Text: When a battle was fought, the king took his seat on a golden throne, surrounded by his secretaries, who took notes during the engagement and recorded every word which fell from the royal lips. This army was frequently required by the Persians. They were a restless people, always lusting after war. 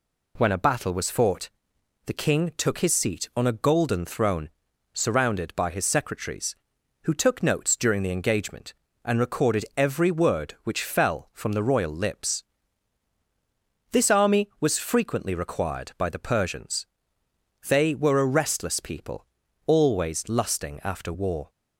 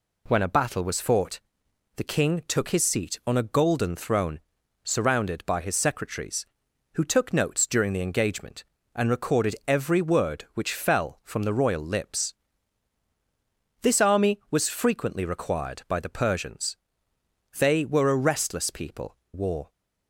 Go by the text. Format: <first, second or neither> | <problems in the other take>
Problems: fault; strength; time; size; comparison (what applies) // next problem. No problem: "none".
first | skips "always lusting after"; at 19.2 s